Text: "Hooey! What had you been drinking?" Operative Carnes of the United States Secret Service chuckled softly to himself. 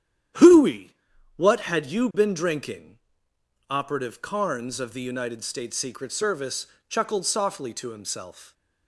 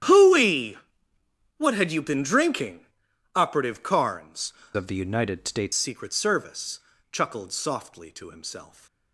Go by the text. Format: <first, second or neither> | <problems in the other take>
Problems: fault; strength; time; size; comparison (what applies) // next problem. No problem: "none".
first | starts louder than the rest; strong; until 1.9 s; 11 dB; strong in the first // changes voice from "of" to "States"; from 4.7 to 5.7 s; 1.0 s long // pauses between "Service" and "chuckled"; slight; at 6.7 s; 0.34 s long; slight in the first